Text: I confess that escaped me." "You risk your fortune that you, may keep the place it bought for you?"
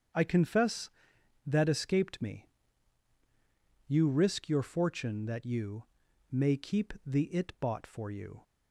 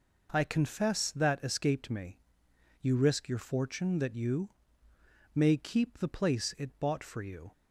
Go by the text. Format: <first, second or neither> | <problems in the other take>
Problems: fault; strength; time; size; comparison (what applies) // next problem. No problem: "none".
second | starts louder than the rest; strong; until 1.7 s; 7.5 dB // skips "place"; at 7.2 s